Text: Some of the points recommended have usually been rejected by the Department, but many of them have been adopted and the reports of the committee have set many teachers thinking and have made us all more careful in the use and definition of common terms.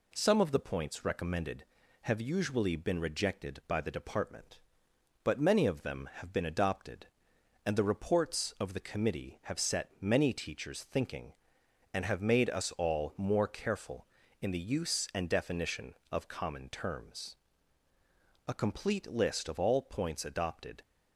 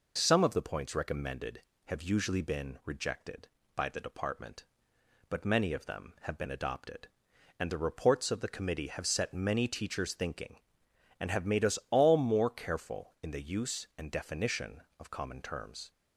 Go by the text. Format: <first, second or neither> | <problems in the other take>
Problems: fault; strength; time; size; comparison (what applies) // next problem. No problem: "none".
second | goes on to say "A complete list of all points adopted"; strong; from 18.4 s on; 2.3 s long